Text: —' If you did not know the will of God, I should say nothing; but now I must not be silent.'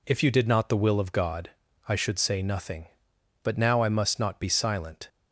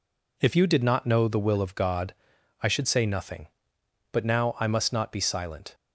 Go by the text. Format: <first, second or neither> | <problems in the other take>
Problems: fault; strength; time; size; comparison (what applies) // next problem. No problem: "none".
second | skips "know"; at 0.6 s